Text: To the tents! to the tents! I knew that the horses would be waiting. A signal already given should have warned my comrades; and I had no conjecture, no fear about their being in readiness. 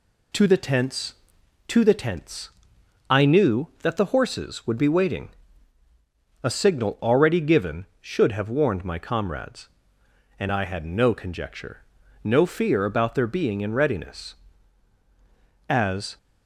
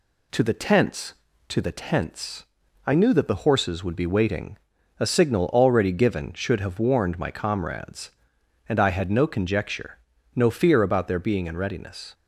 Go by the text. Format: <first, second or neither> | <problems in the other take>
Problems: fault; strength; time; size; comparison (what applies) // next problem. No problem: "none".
second | goes on to say "As"; slight; from 15.6 s on; 0.48 s long